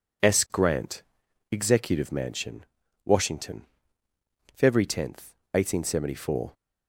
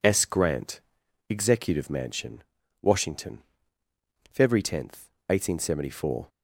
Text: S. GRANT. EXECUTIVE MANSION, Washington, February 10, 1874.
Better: neither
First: none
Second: none

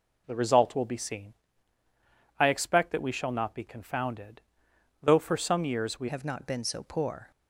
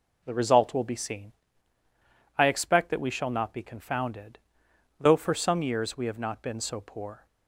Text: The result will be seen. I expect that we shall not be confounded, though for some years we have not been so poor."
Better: second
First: changes voice at "have"; from 6.0 s on; 1.3 s long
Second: none

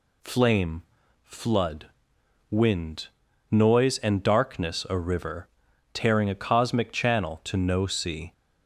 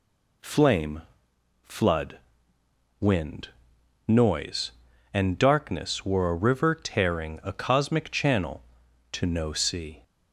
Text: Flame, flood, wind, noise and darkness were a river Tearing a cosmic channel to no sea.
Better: second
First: skips "were"; at 4.8 s // pauses between "river" and "Tearing"; at 5.4 s; 0.44 s long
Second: none

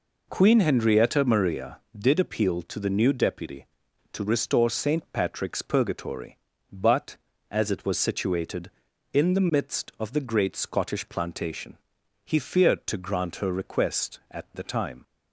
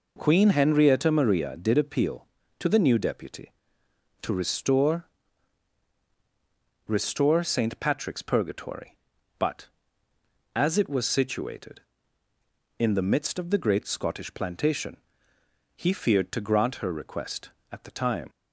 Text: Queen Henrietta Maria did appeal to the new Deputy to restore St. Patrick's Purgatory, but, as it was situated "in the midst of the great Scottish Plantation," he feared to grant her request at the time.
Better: first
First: none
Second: says "restore" twice; at 6.8 s

